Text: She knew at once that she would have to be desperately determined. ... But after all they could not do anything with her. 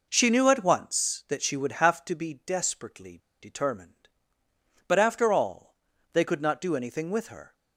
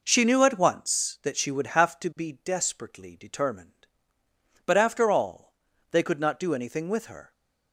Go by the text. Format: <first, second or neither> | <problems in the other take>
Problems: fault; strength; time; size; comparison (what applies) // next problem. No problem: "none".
second | pauses between "desperately" and "determined"; slight; at 3.1 s; 0.23 s long // pauses between "all" and "they"; at 5.6 s; 0.44 s long; also in the second